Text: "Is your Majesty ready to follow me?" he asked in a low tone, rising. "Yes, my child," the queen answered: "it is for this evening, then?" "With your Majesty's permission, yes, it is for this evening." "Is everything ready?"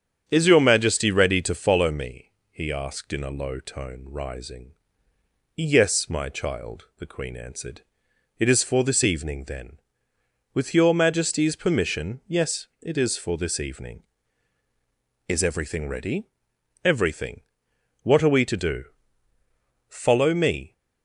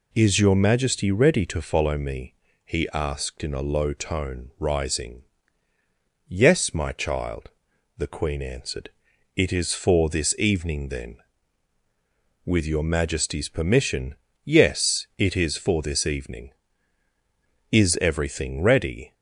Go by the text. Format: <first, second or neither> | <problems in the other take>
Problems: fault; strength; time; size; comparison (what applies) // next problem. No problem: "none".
second | starts louder than the rest; strong; until 1.2 s; 8.5 dB // goes on to say "Everything What are we to do Follow me"; strong; from 16.8 s on; 3.9 s long